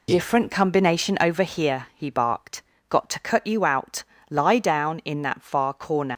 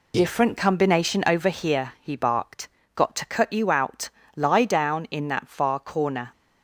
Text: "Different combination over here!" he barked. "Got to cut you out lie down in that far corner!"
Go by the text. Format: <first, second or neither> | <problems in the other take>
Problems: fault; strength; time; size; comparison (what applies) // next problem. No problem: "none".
second | pauses between "out" and "lie"; slight; at 4.0 s; 0.26 s long; slight in the second // leaves "corner" unfinished; at 6.1 s; 100 ms